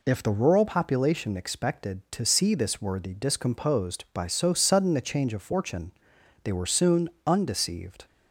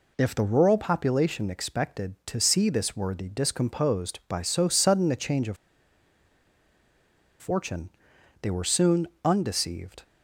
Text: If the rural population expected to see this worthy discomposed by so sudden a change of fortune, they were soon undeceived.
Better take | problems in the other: first | pauses between "of" and "fortune"; strong; at 5.5 s; 1.8 s long // pauses between "soon" and "undeceived"; slight; at 9.0 s; 0.18 s long; slight in the first

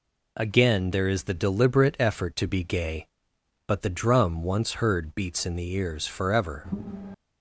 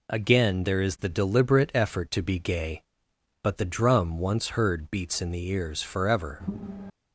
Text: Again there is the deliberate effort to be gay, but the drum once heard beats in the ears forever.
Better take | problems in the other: neither | none

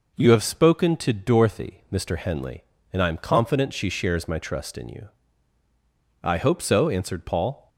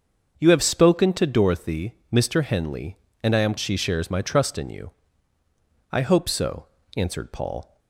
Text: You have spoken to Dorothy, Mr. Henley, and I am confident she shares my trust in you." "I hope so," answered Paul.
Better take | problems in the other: first | starts louder than the rest; until 1.3 s; 6.5 dB // skips "confident"; at 3.5 s

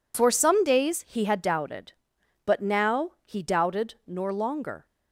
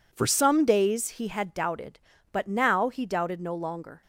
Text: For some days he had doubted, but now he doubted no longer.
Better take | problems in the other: second | pauses between "now" and "he"; slight; at 3.0 s; 0.16 s long // says "nor" for "no"; at 4.0 s

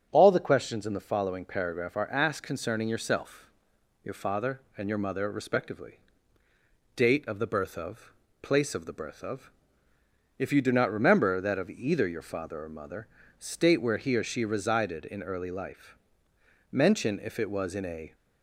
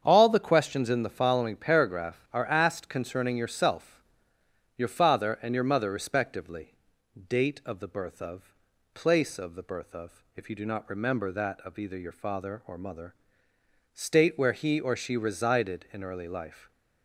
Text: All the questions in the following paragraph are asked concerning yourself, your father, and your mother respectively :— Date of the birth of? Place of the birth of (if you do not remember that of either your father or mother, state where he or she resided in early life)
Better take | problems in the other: second | starts louder than the rest; strong; until 1.1 s; 8 dB; strong in the second // goes on to say "Mention if it was in a"; from 16.7 s on; 1.4 s long

